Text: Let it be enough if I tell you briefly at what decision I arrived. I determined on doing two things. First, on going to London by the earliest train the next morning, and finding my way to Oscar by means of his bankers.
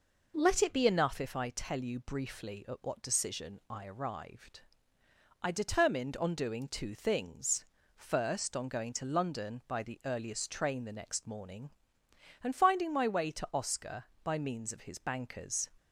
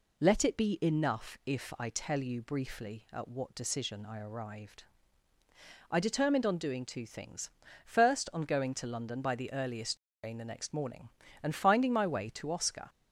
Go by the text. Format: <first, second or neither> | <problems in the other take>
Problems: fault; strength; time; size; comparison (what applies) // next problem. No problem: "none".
first | pauses between "earliest" and "train"; slight; at 9.9 s; 0.24 s long // stops before "by means of his bankers"; at 12.8 s